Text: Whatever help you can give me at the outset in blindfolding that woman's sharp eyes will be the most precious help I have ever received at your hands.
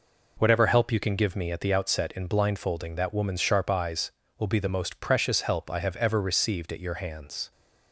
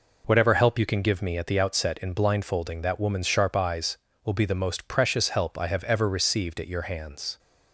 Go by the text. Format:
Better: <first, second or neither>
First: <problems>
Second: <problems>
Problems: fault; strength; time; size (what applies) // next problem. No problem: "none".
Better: neither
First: none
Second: none